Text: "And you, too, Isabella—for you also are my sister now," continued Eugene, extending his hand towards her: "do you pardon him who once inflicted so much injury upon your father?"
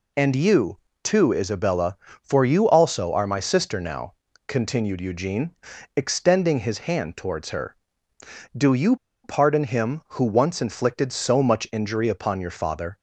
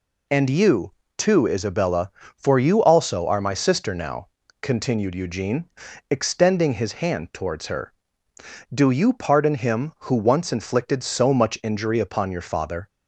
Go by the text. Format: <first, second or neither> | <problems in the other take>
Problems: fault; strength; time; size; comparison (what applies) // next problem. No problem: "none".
second | pauses between "you" and "pardon"; slight; at 8.9 s; 0.27 s long